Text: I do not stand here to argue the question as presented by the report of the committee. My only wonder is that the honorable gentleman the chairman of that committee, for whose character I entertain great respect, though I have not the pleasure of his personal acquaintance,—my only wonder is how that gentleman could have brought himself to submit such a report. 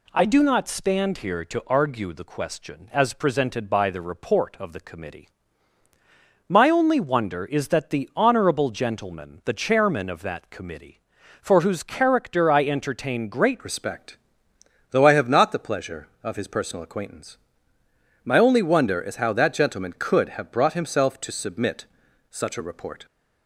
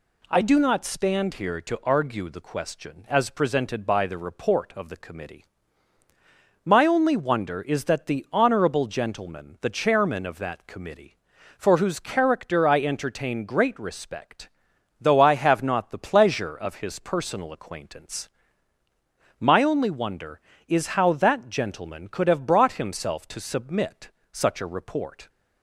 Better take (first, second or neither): second